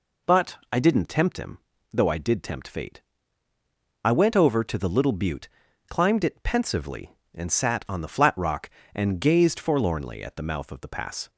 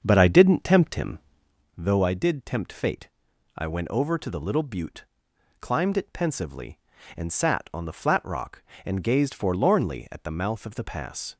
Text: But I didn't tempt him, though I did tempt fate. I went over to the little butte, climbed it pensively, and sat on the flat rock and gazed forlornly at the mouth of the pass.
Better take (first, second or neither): first